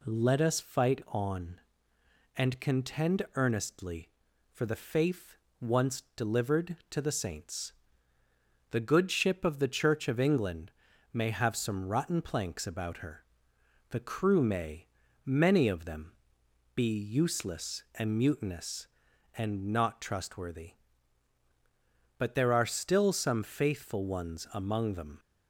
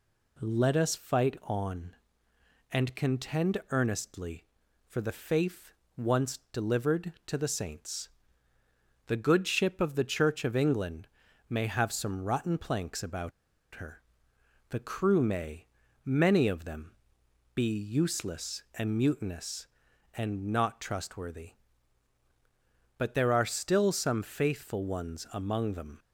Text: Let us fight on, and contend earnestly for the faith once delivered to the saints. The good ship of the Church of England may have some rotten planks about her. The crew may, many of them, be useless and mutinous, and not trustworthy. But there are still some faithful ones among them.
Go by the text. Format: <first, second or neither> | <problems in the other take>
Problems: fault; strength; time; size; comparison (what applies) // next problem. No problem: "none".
first | pauses between "faith" and "once"; slight; at 5.7 s; 0.24 s long; slight in the first // pauses between "England" and "may"; at 11.0 s; 0.42 s long; also in the first // pauses between "about" and "her"; at 13.3 s; 0.43 s long